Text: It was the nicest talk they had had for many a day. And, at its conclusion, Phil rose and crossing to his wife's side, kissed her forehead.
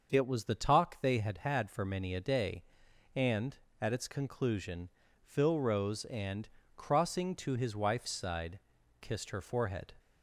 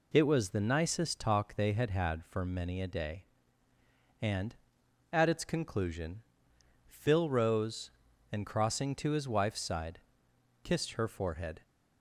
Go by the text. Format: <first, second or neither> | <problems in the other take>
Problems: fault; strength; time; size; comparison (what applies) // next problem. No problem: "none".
second | starts louder than the rest; until 1.1 s; 6.5 dB // skips "nicest"; at 0.5 s // pauses between "and" and "crossing"; slight; at 6.4 s; 0.26 s long